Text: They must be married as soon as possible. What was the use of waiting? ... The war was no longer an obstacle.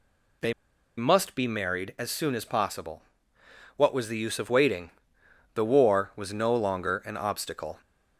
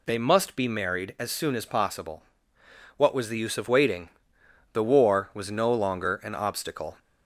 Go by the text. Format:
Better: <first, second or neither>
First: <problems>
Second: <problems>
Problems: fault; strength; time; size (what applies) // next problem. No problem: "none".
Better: second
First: pauses between "They" and "must"; at 0.5 s; 0.45 s long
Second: none